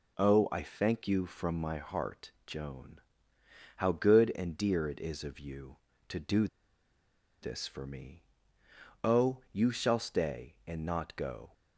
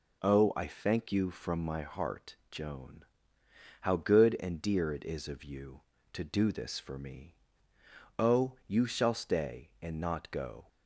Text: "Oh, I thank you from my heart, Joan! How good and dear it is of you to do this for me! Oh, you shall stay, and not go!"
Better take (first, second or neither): second